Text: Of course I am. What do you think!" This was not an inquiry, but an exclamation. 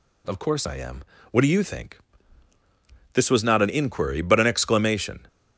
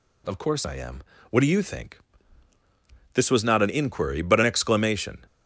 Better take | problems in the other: neither | none

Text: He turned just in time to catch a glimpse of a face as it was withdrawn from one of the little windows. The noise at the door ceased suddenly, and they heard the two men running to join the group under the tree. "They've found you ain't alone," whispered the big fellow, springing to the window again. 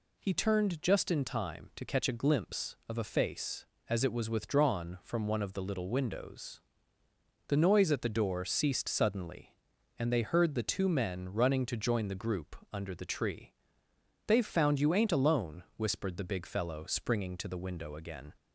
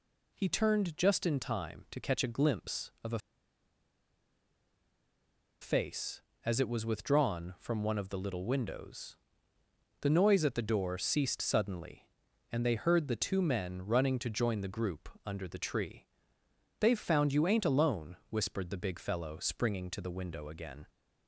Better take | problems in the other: first | pauses between "a" and "face"; strong; at 3.1 s; 2.4 s long // pauses between "group" and "under"; slight; at 15.0 s; 0.16 s long; slight in the first

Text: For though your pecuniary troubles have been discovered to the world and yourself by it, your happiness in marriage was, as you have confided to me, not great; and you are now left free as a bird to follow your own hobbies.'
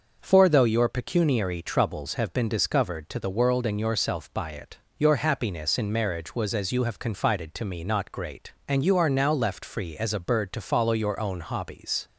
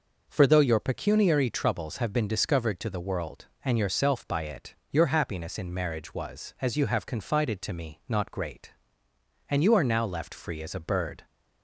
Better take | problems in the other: first | stops before "to follow your own hobbies"; at 11.2 s

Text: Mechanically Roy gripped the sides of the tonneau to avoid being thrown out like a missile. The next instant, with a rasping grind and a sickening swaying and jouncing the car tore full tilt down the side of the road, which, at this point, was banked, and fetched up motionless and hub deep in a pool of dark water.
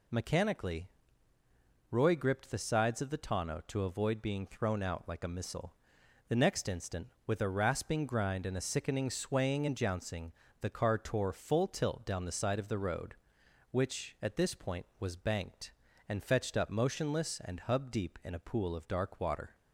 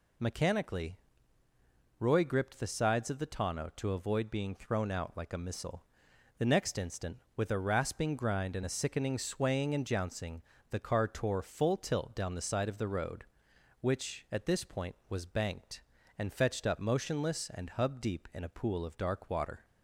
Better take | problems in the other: neither | pauses between "Mechanically" and "Roy"; the same in both // pauses between "jouncing" and "the"; slight; the same in both

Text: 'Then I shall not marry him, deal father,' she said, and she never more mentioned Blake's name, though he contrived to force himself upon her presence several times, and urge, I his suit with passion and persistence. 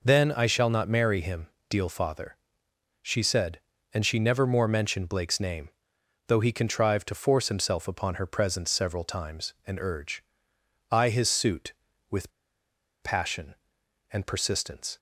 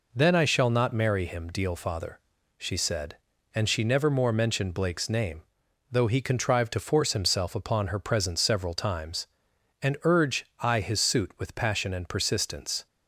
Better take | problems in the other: second | pauses between "with" and "passion"; noticeable; at 12.3 s; 0.72 s long

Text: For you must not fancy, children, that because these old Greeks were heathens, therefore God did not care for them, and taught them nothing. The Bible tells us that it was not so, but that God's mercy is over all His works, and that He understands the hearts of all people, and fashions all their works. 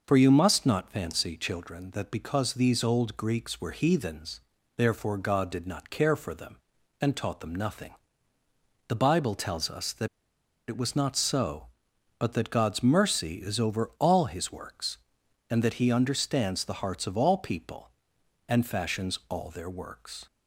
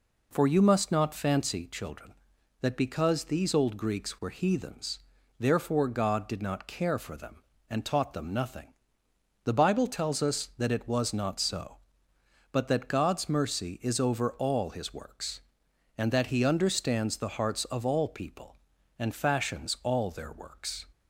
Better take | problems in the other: second | pauses between "that" and "it"; noticeable; at 10.0 s; 0.61 s long

